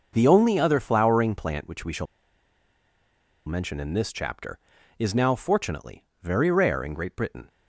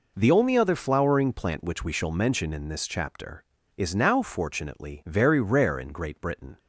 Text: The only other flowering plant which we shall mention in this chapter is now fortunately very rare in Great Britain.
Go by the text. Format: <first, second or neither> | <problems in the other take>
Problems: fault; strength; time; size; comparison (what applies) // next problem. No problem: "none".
second | pauses between "shall" and "mention"; strong; at 2.0 s; 1.4 s long // pauses between "fortunately" and "very"; slight; at 6.0 s; 0.16 s long